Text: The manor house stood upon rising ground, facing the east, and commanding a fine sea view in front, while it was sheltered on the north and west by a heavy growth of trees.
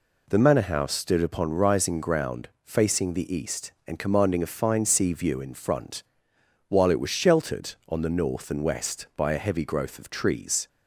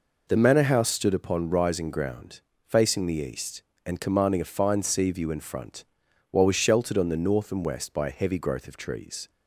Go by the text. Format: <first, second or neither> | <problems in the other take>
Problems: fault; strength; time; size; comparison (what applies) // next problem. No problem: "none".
first | skips "it"; at 6.4 s